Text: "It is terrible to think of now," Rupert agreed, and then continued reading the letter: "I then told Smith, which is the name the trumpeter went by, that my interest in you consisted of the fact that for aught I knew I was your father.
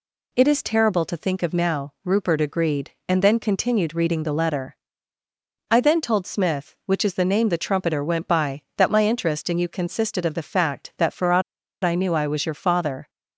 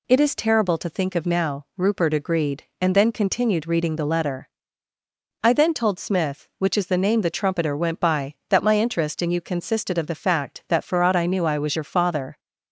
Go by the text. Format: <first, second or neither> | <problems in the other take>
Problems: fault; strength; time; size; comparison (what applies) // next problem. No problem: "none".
second | pauses between "aught" and "I"; at 11.4 s; 0.41 s long